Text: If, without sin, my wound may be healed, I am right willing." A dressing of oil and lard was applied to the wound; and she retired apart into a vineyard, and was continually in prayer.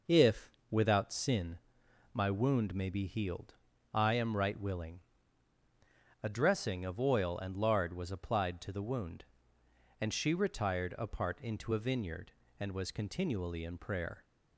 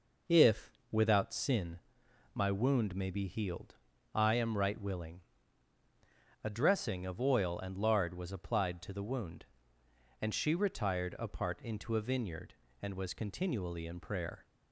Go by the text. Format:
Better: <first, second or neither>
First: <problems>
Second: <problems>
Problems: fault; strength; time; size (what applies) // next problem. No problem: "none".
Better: neither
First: none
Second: none